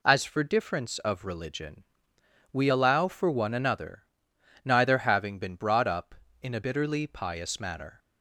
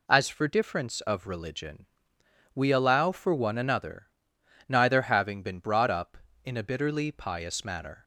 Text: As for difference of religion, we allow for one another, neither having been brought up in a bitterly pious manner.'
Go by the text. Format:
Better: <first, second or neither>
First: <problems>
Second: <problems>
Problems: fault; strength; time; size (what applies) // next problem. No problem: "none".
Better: neither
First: none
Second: none